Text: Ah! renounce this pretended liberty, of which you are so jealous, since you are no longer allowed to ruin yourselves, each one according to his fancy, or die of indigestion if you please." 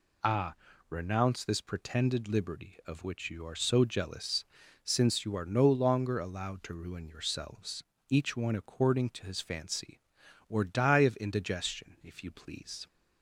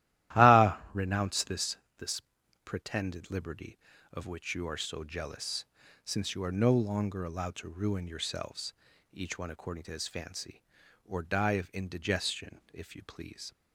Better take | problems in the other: first | starts louder than the rest; strong; until 1.4 s; 14 dB // says "this" twice; at 1.9 s

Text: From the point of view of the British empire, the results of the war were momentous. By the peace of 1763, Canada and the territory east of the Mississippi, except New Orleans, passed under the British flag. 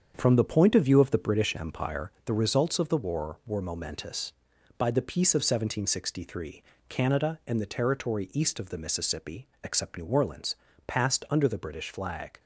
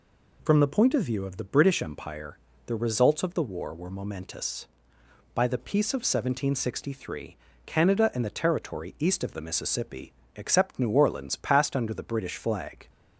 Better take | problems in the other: second | gets quieter; throughout; 7 dB

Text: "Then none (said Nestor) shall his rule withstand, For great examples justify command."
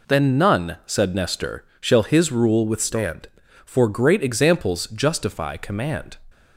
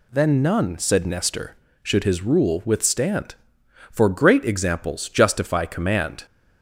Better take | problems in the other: first | says "should" for "shall"; at 1.8 s

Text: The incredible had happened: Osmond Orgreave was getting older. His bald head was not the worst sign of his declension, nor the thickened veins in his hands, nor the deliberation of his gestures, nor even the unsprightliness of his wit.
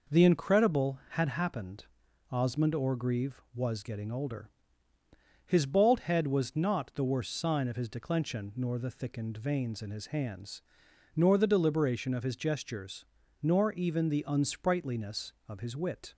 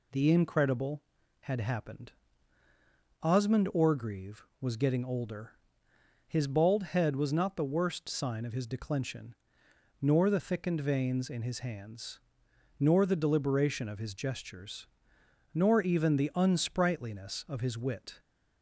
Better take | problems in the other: neither | none

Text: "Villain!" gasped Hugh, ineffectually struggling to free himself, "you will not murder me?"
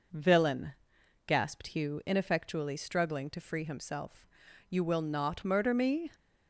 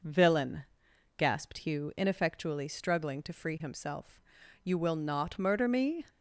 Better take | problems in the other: neither | none

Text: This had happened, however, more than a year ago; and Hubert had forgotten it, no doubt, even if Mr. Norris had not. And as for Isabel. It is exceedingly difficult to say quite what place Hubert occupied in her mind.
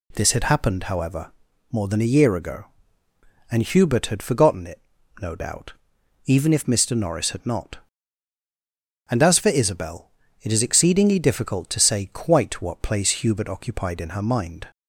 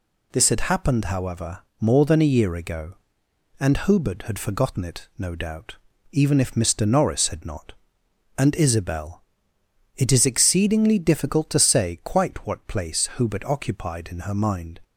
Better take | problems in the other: first | skips "as for"; at 8.5 s

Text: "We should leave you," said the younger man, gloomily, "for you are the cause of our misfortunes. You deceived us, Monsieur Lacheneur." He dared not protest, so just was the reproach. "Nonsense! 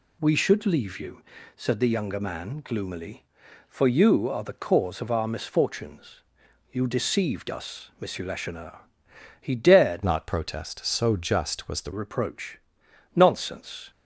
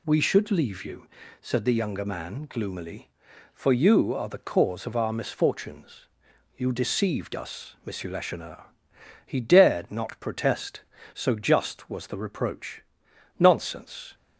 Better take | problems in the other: second | changes voice from "not" to "the"; from 10.0 to 11.9 s; 1.9 s long

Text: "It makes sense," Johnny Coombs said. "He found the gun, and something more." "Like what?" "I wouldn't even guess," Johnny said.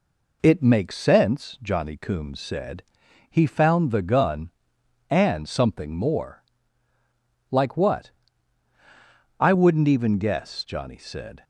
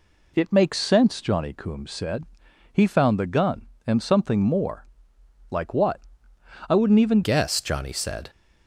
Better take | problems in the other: first | changes voice at "guess"; from 7.2 s on; 1.0 s long

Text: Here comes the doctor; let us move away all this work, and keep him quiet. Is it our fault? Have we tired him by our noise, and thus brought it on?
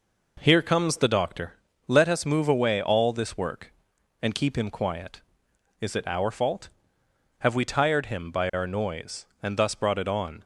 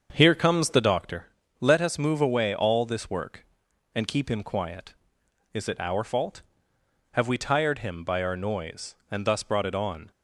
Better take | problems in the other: first | starts louder than the rest; until 1.0 s; 7 dB

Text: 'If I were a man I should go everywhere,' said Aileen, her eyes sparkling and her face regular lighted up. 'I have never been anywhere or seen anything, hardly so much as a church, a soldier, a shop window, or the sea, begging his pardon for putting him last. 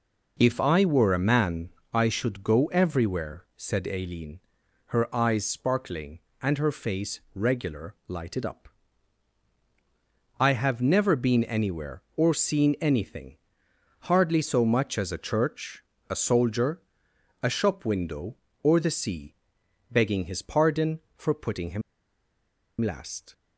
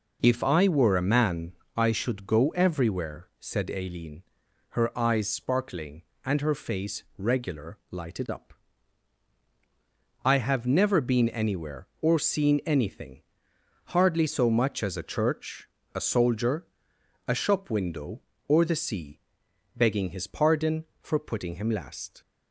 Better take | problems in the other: second | pauses between "man" and "I"; slight; at 1.6 s; 0.22 s long; slight in the second // pauses between "him" and "last"; at 21.8 s; 0.99 s long

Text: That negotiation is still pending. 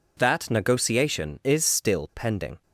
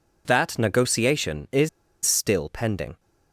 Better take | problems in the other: first | pauses between "is" and "still"; at 1.6 s; 0.36 s long

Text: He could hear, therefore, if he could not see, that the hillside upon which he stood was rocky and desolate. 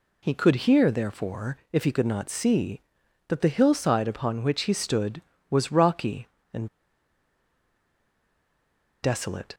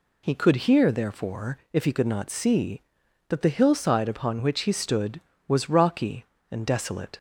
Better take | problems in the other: second | pauses between "and" and "desolate"; strong; at 6.6 s; 2.3 s long

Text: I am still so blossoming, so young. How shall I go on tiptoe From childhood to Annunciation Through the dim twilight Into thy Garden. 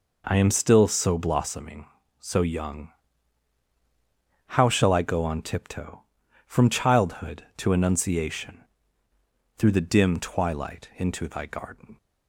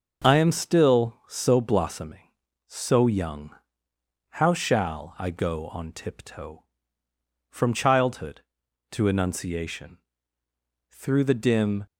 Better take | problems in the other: first | starts louder than the rest; until 1.3 s; 6 dB // pauses between "Annunciation" and "Through"; noticeable; at 9.9 s; 0.94 s long; noticeable in the first // stops before "twilight Into thy Garden"; at 11.8 s

